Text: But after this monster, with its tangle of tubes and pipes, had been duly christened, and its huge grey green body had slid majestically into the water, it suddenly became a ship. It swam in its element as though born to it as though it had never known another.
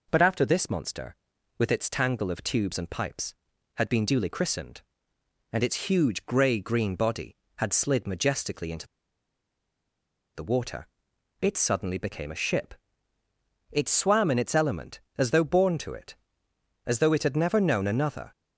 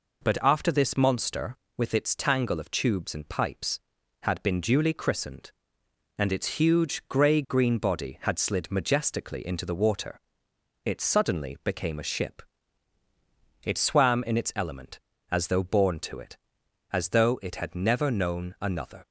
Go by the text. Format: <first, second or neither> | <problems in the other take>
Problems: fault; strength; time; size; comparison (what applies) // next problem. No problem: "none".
second | pauses between "into" and "the"; strong; at 8.8 s; 1.4 s long